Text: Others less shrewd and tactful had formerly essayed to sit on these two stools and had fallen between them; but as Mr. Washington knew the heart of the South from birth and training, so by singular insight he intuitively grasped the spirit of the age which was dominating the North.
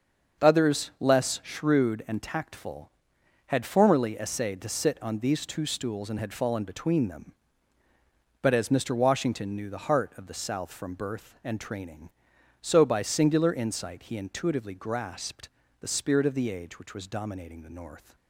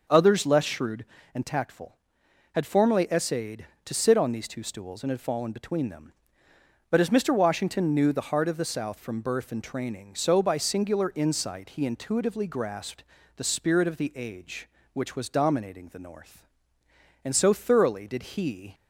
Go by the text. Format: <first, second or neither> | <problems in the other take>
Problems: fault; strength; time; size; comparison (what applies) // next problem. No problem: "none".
first | starts louder than the rest; noticeable; until 1.3 s; 6 dB; also in the first // pauses between "grasped" and "the"; slight; at 13.0 s; 0.32 s long; slight in the first // goes on to say "And so thoroughly did he"; from 17.2 s on; 1.4 s long